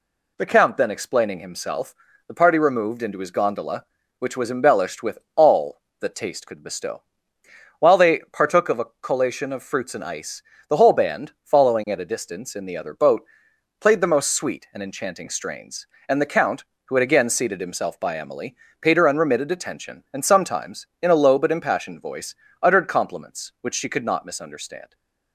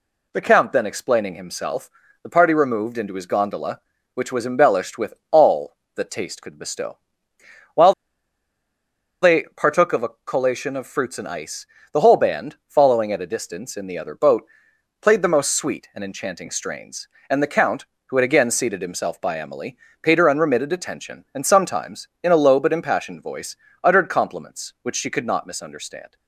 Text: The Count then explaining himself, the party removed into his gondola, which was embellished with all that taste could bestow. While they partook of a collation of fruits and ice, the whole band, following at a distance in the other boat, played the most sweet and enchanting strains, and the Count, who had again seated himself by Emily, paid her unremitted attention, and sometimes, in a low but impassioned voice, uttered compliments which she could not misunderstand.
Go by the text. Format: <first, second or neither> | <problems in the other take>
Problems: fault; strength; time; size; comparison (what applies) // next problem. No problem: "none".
first | pauses between "with" and "all"; slight; at 5.1 s; 0.18 s long; slight in the first // pauses between "While" and "they"; strong; at 7.9 s; 1.3 s long